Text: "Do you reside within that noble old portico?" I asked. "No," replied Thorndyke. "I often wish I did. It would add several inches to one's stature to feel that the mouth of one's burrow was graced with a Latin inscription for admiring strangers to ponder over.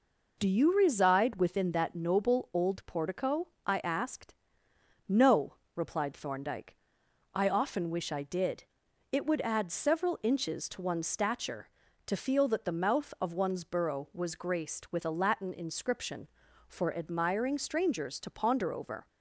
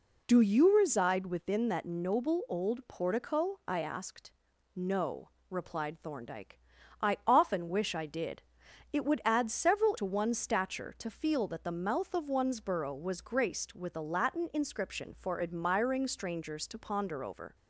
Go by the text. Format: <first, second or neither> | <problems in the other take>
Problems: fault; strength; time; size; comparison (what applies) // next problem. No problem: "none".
first | skips "inches"; at 9.9 s